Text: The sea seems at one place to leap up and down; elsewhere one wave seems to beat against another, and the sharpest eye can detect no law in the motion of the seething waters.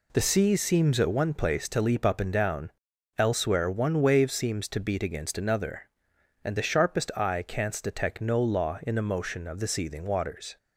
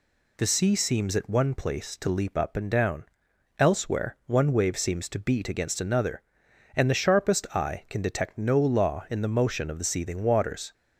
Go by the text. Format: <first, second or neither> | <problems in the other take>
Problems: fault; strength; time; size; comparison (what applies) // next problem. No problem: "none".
second | says "canst" for "can"; at 7.4 s